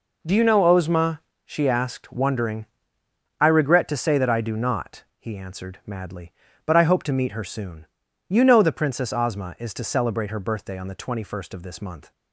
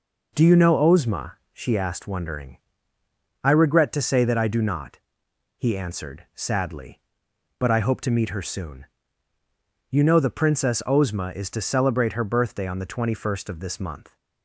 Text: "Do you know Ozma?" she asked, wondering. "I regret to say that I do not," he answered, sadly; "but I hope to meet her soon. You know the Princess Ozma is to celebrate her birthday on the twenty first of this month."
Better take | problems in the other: second | says "madly" for "sadly"; at 5.8 s

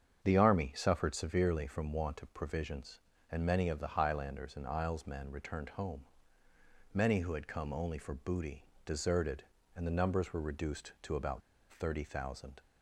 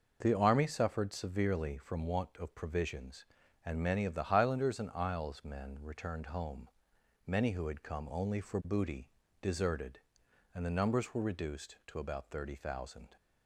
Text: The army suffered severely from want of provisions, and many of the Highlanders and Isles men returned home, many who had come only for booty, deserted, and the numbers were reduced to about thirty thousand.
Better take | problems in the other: second | starts louder than the rest; strong; until 1.2 s; 7.5 dB // pauses between "about" and "thirty"; slight; at 11.4 s; 0.29 s long

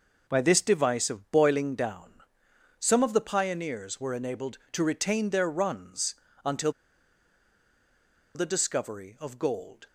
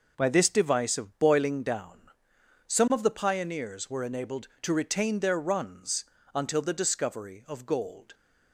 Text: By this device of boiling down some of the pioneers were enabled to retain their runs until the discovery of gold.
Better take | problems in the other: second | pauses between "down" and "some"; noticeable; at 2.1 s; 0.68 s long; noticeable in the second // pauses between "runs" and "until"; slight; at 6.1 s; 0.32 s long; slight in the second // pauses between "until" and "the"; strong; at 6.6 s; 1.6 s long

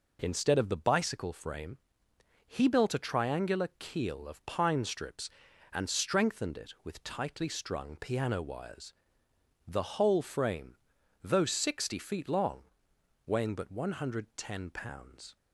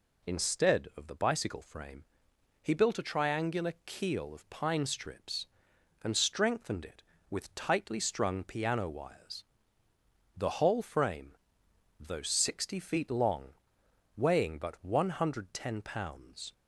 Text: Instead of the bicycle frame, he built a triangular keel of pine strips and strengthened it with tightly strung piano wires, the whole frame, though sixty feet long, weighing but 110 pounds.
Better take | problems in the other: neither | none

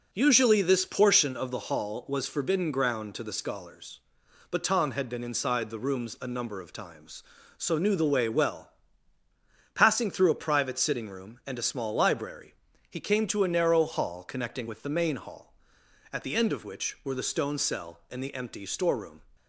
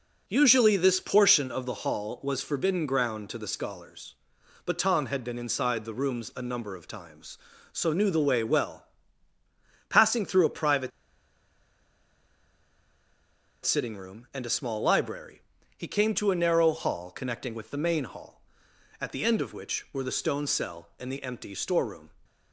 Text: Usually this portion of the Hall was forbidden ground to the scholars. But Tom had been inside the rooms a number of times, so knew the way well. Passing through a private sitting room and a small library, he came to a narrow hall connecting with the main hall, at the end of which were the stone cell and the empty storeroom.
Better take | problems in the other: first | pauses between "private" and "sitting"; strong; at 10.9 s; 2.7 s long

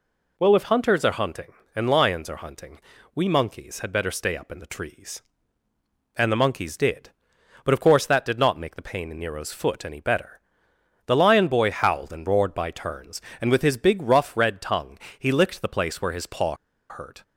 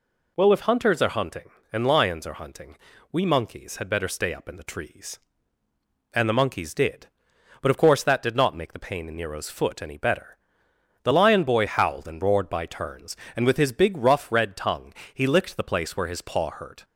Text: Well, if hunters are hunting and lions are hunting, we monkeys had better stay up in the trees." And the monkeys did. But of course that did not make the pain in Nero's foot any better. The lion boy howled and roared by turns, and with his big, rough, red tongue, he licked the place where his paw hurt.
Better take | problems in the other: second | pauses between "paw" and "hurt"; slight; at 16.5 s; 0.34 s long

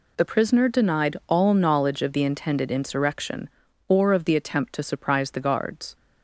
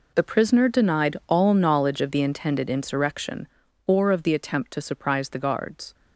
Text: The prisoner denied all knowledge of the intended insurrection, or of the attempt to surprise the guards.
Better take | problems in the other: first | gets quieter; strong; throughout; 15 dB

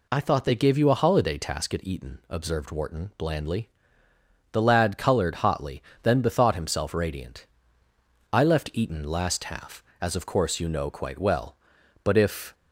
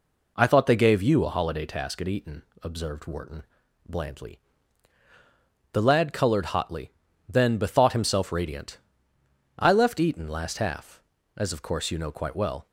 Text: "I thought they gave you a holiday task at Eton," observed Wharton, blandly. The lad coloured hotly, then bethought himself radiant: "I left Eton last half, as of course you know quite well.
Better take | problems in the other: second | goes on to say "But if"; from 12.0 s on; 0.50 s long

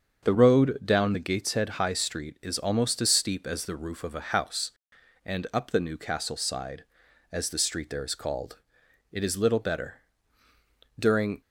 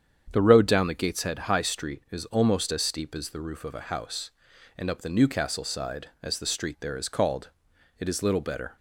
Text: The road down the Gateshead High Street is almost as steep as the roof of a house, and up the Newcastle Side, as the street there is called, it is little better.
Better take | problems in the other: second | starts louder than the rest; strong; until 1.3 s; 7 dB; strong in the second // goes on to say "During"; slight; from 10.9 s on; 0.42 s long

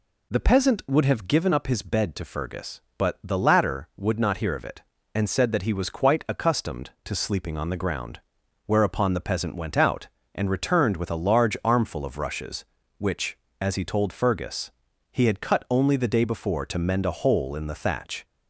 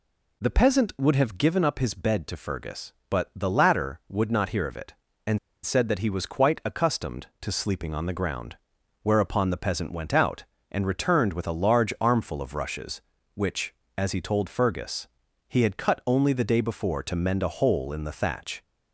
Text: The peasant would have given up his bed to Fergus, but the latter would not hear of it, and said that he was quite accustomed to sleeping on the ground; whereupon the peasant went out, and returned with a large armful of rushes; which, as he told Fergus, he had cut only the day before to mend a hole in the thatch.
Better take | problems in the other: first | pauses between "and" and "said"; slight; at 5.3 s; 0.25 s long

